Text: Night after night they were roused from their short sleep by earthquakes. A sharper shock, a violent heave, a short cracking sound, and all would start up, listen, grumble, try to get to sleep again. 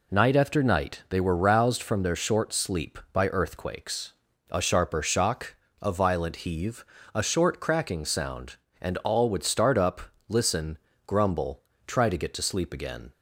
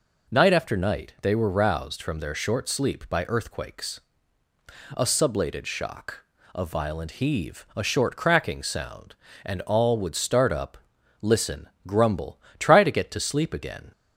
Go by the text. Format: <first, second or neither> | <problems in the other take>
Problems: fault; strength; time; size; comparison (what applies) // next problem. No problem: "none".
first | says "sublated" for "sharper"; at 5.0 s